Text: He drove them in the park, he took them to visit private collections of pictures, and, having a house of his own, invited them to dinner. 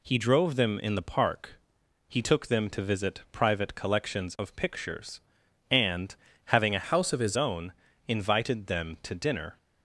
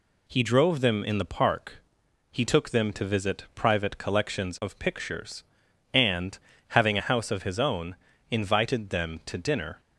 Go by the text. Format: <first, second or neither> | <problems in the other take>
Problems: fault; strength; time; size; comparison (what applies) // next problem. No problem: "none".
second | changes voice from "house" to "his"; from 6.8 to 7.3 s; 0.5 s long